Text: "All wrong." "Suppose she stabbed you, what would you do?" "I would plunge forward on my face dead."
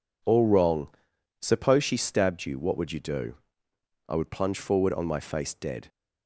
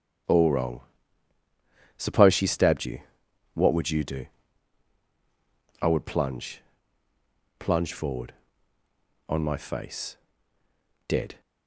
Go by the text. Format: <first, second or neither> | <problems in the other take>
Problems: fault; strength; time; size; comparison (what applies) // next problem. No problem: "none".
first | starts louder than the rest; strong; until 2.4 s; 9 dB // says "plunge" twice; at 7.5 s // pauses between "face" and "dead"; noticeable; at 10.1 s; 0.92 s long